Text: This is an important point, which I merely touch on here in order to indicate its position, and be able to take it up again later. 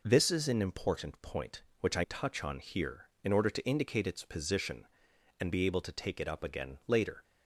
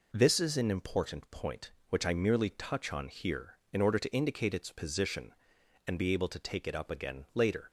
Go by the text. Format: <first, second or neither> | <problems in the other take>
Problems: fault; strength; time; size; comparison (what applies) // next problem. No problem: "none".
second | skips "merely"; at 2.0 s